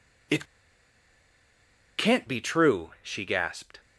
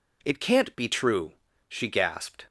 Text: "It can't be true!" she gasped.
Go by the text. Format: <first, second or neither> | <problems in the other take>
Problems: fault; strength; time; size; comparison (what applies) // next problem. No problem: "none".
second | pauses between "It" and "can't"; strong; at 0.4 s; 1.5 s long